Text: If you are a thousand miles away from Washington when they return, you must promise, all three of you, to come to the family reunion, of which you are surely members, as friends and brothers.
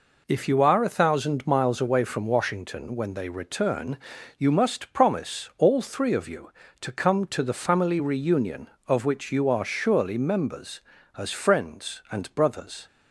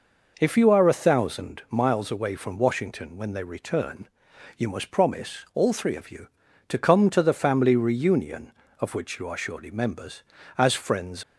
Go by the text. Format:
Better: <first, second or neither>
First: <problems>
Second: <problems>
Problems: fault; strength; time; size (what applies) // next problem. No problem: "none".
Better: first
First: none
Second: stops before "and brothers"; at 11.2 s